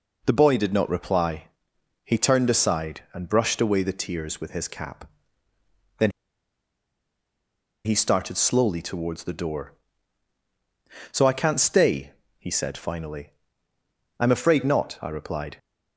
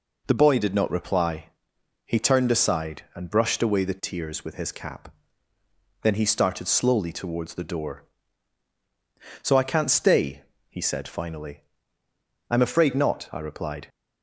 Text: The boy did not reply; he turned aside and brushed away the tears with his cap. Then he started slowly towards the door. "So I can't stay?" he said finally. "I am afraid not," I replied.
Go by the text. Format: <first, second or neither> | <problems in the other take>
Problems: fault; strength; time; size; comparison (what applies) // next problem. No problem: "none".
second | pauses between "Then" and "he"; strong; at 6.1 s; 1.7 s long